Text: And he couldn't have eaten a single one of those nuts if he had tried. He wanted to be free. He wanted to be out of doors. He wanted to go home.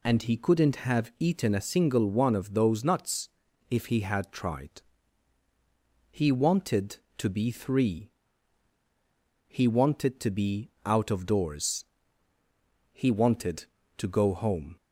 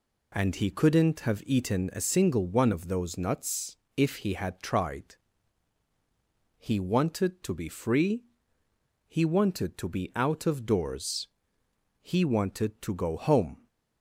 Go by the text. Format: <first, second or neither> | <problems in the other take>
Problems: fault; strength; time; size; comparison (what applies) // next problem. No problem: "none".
second | pauses between "nuts" and "if"; at 3.2 s; 0.42 s long; slight in the second // says "three" for "free"; at 7.5 s